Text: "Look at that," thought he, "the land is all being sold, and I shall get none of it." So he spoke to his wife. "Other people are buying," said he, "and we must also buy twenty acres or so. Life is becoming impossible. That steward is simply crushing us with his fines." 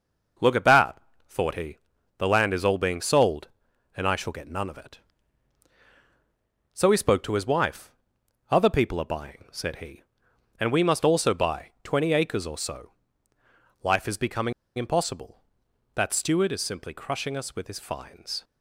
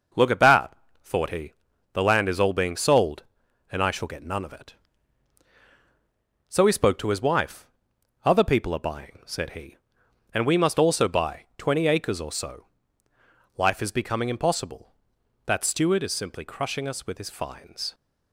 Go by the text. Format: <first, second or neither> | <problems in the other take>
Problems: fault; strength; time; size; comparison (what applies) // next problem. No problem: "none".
second | pauses between "becoming" and "impossible"; slight; at 14.5 s; 0.24 s long